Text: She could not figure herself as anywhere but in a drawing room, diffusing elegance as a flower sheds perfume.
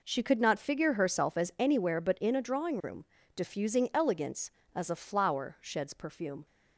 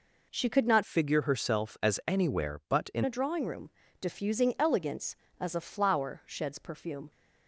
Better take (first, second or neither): first